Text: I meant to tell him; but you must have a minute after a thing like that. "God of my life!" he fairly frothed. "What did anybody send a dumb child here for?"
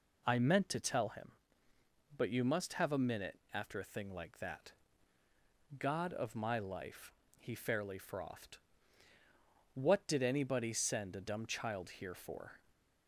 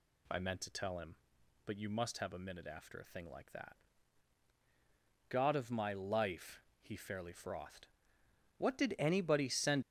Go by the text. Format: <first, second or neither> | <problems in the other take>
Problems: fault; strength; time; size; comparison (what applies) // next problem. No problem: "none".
first | stops before "a dumb child here for"; at 9.8 s